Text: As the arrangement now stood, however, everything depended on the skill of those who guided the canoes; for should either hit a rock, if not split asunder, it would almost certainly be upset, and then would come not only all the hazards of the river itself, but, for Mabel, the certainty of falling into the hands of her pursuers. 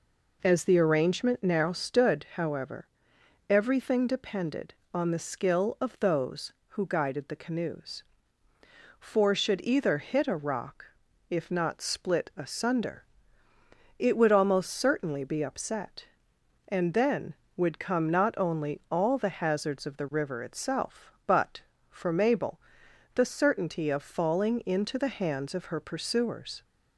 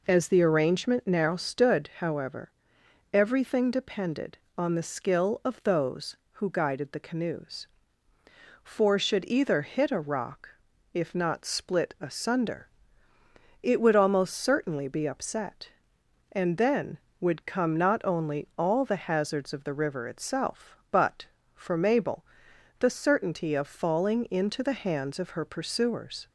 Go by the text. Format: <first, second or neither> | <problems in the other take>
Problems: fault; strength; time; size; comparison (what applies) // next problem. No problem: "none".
neither | none